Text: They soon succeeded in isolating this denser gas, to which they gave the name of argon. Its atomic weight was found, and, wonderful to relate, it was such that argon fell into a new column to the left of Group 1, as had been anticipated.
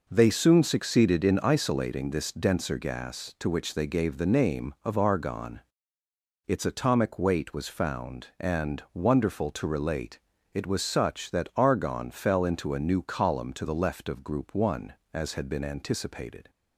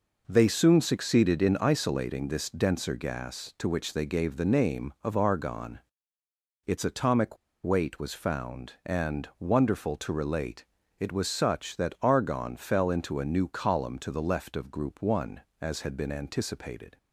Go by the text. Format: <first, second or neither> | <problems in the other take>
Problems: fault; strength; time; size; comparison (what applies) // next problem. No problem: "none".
first | pauses between "atomic" and "weight"; slight; at 7.3 s; 0.26 s long